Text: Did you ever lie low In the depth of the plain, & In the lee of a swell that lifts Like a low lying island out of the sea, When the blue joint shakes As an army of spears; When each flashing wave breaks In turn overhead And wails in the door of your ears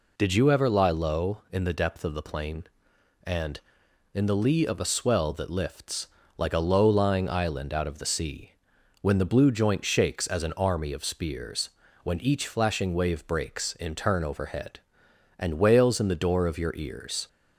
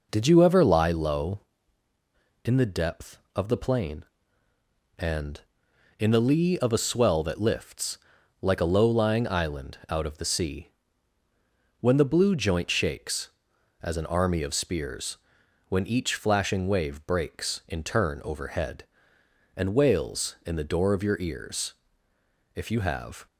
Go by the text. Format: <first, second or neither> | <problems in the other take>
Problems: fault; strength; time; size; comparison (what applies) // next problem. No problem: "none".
first | pauses between "lifts" and "Like"; noticeable; at 7.9 s; 0.46 s long; slight in the first // goes on to say "If you have"; noticeable; from 22.5 s on; 0.70 s long